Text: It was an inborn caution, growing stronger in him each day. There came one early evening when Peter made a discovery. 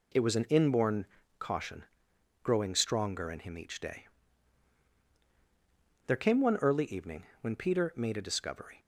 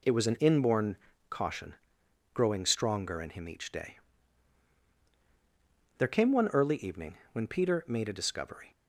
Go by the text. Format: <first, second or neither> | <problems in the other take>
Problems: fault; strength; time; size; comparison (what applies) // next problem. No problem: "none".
neither | pauses between "inborn" and "caution"; slight; the same in both // pauses between "evening" and "when"; slight; the same in both